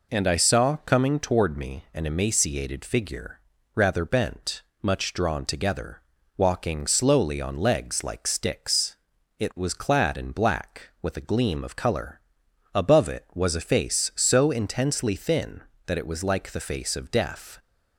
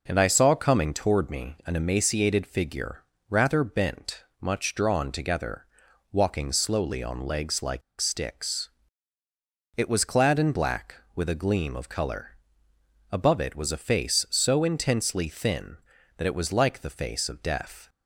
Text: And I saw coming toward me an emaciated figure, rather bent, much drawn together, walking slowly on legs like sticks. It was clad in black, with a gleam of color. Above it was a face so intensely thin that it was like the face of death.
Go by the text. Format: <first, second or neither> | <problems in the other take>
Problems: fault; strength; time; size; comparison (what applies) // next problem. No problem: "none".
first | pauses between "like" and "sticks"; slight; at 7.8 s; 0.19 s long